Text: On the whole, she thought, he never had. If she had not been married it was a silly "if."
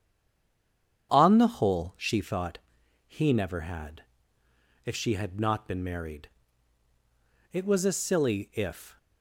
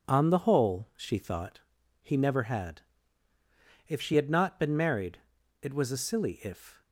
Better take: second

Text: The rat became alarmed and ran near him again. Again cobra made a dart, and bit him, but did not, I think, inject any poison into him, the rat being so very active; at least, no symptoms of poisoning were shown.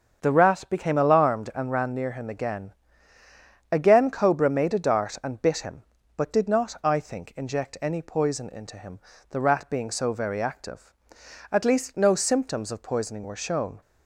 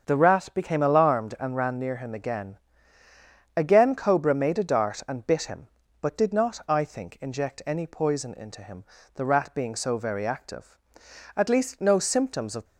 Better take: first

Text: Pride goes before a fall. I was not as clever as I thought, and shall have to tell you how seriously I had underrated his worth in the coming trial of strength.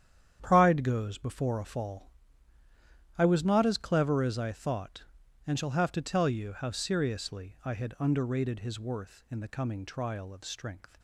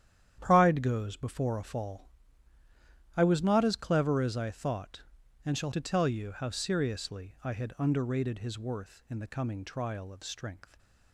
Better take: first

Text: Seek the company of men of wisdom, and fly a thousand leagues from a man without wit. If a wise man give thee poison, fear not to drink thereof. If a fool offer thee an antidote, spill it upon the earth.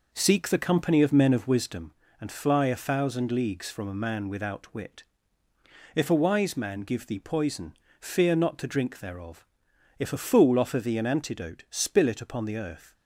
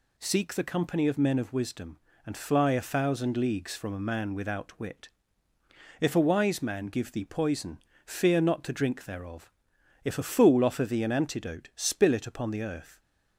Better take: second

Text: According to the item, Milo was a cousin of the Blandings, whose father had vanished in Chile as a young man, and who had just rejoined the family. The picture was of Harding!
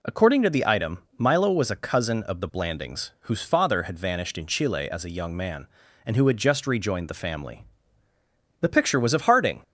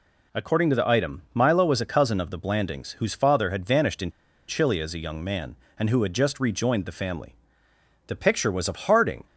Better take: first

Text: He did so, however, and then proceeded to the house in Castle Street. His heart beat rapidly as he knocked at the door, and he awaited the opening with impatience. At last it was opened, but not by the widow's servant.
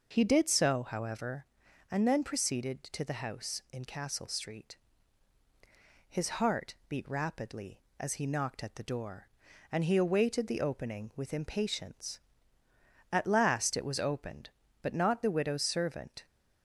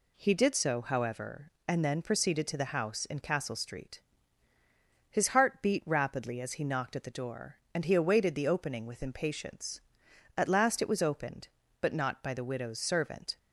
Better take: second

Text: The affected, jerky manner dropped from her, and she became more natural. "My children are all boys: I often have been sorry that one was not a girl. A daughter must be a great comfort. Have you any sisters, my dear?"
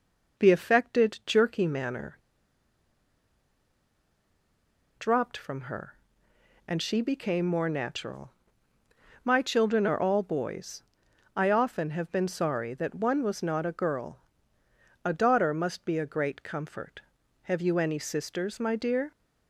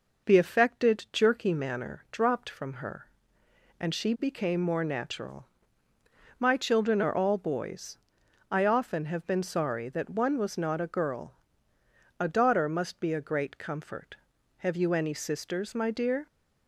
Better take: second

